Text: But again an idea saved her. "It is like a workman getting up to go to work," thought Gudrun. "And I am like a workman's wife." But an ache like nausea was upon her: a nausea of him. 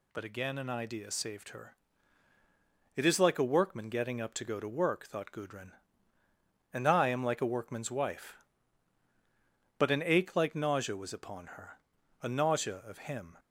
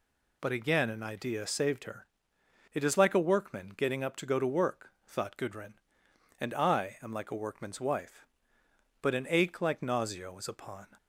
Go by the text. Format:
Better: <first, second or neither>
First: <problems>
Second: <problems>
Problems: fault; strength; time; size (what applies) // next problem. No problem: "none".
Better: first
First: none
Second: stops before "her a nausea of him"; at 10.9 s